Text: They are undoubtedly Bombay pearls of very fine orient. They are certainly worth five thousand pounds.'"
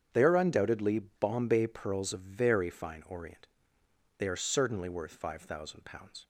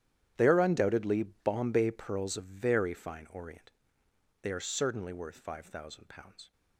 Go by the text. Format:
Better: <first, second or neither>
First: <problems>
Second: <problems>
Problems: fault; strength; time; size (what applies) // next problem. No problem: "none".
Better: first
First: starts louder than the rest; strong; until 1.1 s; 8 dB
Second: gets quieter; strong; throughout; 16 dB // starts louder than the rest; strong; until 1.3 s; 10.5 dB